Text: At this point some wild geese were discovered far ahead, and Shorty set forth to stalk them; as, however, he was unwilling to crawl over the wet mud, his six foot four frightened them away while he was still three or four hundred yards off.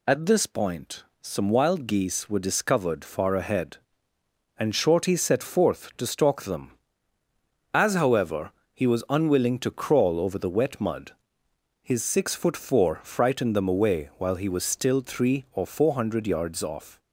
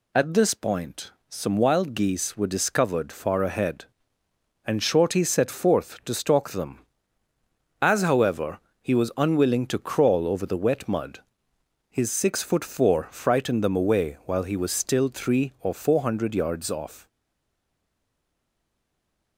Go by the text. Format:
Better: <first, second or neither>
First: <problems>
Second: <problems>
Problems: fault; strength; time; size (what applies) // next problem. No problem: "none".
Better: first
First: pauses between "point" and "some"; slight; at 1.0 s; 0.18 s long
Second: pauses between "point" and "some"; slight; at 1.1 s; 0.18 s long // stays silent after the last word; from 17.0 s on; 2.3 s long